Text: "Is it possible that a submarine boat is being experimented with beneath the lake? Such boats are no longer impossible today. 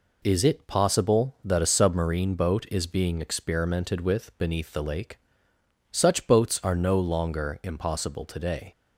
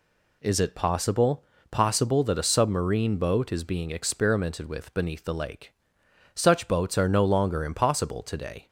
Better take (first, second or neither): first